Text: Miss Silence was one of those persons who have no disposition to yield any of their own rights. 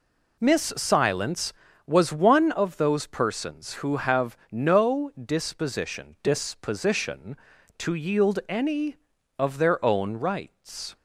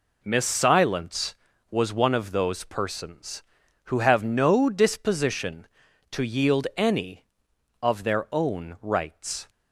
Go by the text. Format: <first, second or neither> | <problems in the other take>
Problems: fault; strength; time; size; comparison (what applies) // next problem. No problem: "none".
second | says "disposition" twice; at 6.2 s